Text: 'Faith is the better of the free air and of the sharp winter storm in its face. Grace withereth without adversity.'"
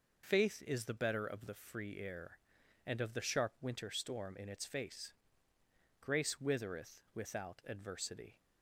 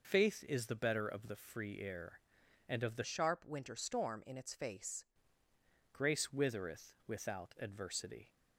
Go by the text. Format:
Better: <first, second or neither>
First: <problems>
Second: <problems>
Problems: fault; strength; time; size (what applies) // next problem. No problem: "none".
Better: first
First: none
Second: changes voice from "sharp" to "face"; from 3.0 to 5.0 s; 2.0 s long